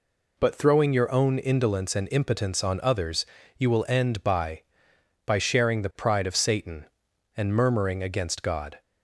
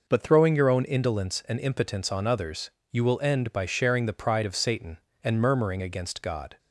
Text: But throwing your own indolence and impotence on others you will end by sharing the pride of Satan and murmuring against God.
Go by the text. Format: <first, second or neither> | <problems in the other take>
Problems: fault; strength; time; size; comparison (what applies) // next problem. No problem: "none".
second | pauses between "others" and "you"; slight; at 3.2 s; 0.32 s long; slight in the second // says "by" twice; at 5.2 s